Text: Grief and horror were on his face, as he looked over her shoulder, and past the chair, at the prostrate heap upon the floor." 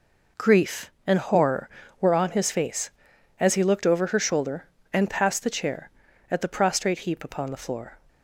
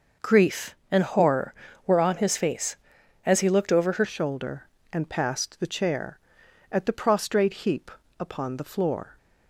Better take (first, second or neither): first